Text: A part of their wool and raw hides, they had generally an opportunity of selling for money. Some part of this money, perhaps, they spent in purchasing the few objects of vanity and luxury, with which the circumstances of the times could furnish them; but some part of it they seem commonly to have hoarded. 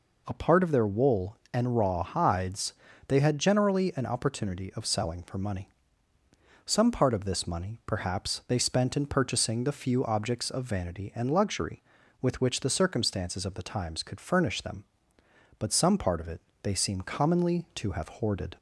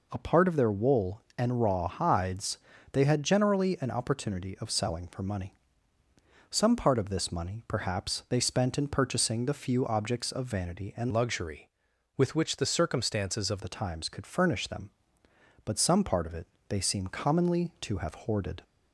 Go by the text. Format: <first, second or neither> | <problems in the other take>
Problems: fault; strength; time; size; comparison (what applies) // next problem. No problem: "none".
first | changes voice from "luxury" to "of"; from 11.1 to 13.6 s; 2.5 s long // pauses between "it" and "they"; slight; at 16.4 s; 0.22 s long; slight in the first